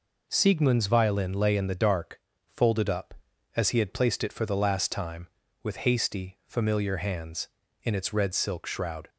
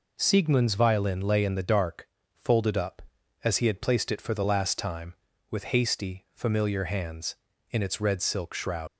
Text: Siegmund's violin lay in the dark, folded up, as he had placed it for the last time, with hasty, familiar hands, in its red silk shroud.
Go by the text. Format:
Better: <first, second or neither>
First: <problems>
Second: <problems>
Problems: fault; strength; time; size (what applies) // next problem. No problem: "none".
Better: first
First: none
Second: leaves "shroud" unfinished; at 8.8 s; 90 ms